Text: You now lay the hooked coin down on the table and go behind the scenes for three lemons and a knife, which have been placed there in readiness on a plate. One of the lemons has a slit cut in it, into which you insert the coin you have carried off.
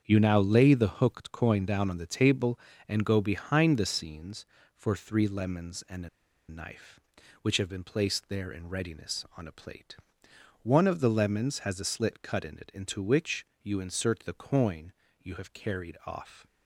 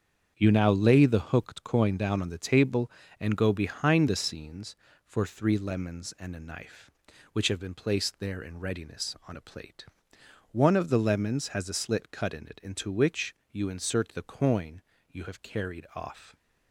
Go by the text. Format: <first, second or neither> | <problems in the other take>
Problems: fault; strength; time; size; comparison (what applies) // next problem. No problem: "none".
second | starts louder than the rest; strong; until 1.0 s; 7.5 dB; strong in the second // pauses between "a" and "knife"; at 6.0 s; 0.40 s long // pauses between "which" and "you"; slight; at 13.4 s; 0.16 s long; slight in the second // pauses between "coin" and "you"; slight; at 14.9 s; 0.28 s long; slight in the second